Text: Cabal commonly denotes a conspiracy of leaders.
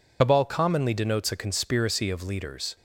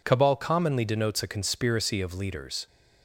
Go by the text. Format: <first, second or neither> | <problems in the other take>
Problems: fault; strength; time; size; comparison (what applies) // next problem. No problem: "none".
second | loses the start of "Cabal"; at 0.2 s; 70 ms